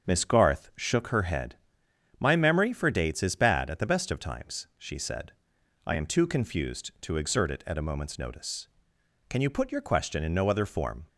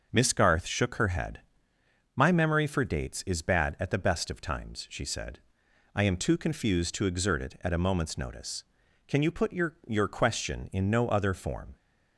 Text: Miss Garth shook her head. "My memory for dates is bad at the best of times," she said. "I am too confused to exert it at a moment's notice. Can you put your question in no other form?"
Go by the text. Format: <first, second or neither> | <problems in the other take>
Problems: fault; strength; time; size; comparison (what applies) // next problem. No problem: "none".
first | starts louder than the rest; until 1.1 s; 6.5 dB; also in the first // says "your" twice; at 9.8 s